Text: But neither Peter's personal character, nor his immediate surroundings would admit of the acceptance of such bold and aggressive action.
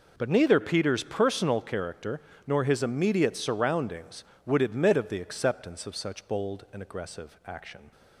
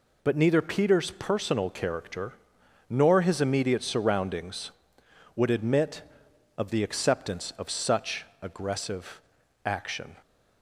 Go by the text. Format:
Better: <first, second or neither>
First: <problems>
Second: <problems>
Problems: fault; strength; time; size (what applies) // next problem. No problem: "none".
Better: first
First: none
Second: skips "bold and"; at 8.3 s // pauses between "aggressive" and "action"; at 9.2 s; 0.44 s long